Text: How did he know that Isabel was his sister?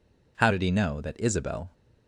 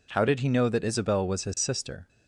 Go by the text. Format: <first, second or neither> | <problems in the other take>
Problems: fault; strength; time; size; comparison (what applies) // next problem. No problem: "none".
second | stops before "was his sister"; at 1.7 s